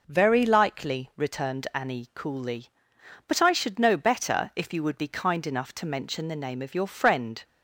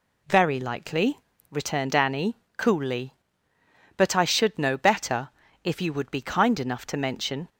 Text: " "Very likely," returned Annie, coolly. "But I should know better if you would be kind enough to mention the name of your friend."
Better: first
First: none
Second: pauses between "better" and "if"; slight; at 5.2 s; 0.36 s long // stops before "the name of your friend"; at 7.4 s

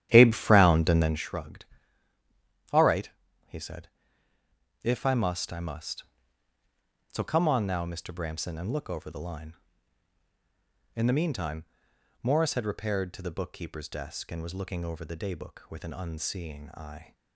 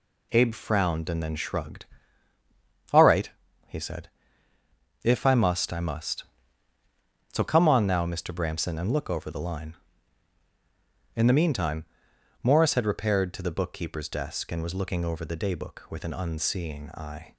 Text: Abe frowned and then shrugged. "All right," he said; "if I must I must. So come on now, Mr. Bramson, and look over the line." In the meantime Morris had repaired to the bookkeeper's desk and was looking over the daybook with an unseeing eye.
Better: second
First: starts louder than the rest; strong; until 1.2 s; 11.5 dB // pauses between "meantime" and "Morris"; noticeable; at 11.6 s; 0.56 s long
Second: pauses between "meantime" and "Morris"; noticeable; at 11.8 s; 0.56 s long

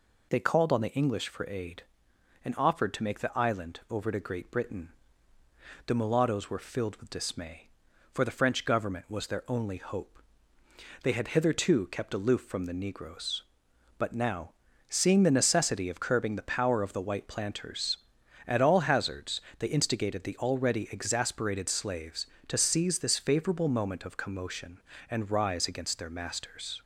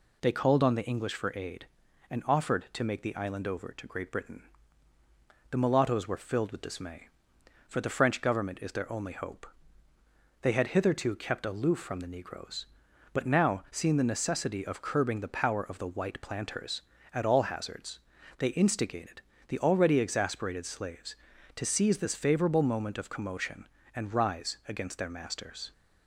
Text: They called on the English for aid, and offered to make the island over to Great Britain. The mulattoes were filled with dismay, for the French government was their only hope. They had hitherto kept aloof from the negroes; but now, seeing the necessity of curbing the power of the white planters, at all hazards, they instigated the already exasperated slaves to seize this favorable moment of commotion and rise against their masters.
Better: first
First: none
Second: says "is" for "was"; at 8.5 s // pauses between "instigated" and "the"; slight; at 19.2 s; 0.28 s long

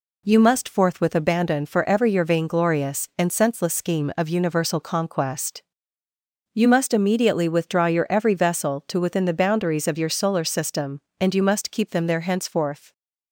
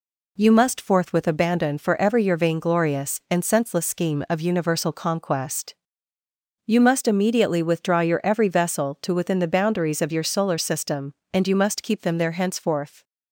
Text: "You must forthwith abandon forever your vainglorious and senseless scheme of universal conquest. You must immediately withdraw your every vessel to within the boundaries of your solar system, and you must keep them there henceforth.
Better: neither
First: none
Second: none

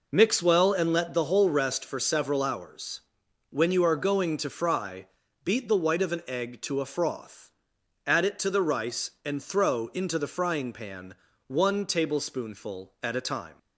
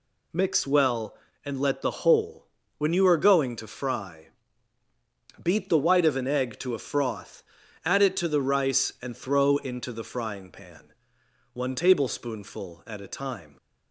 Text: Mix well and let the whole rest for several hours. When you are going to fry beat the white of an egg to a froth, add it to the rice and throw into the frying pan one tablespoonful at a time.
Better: first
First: pauses between "fry" and "beat"; at 5.0 s; 0.38 s long // pauses between "pan" and "one"; slight; at 11.1 s; 0.34 s long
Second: skips "rest for several hours"; at 2.6 s // pauses between "fry" and "beat"; at 4.2 s; 1.1 s long // pauses between "pan" and "one"; noticeable; at 10.9 s; 0.60 s long

